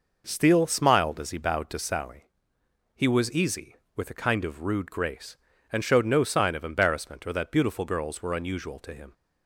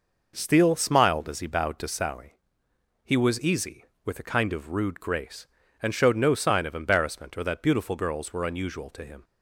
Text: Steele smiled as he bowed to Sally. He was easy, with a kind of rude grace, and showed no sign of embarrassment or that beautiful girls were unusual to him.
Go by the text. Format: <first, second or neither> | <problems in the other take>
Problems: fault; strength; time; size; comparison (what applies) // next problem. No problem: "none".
neither | none